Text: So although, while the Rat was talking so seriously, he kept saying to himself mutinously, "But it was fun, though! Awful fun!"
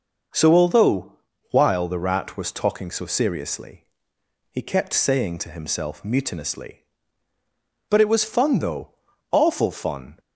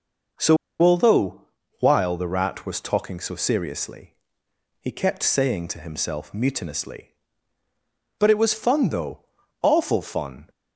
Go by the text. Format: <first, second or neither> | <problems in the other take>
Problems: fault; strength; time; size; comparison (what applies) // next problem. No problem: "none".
first | pauses between "So" and "although"; slight; at 0.5 s; 0.25 s long